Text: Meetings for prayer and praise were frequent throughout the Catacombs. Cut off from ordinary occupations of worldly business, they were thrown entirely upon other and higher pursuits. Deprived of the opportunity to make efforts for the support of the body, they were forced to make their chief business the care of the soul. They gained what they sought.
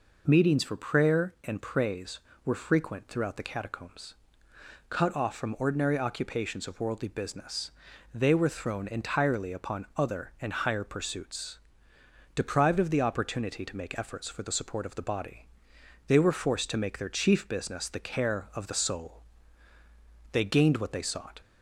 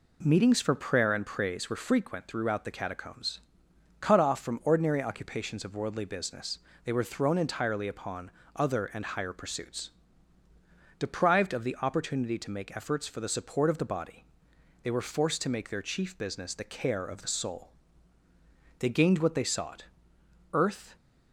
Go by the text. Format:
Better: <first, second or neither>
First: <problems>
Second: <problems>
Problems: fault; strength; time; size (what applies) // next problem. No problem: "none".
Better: first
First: none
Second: pauses between "upon" and "other"; slight; at 8.2 s; 0.26 s long // goes on to say "Earth"; slight; from 20.5 s on; 0.42 s long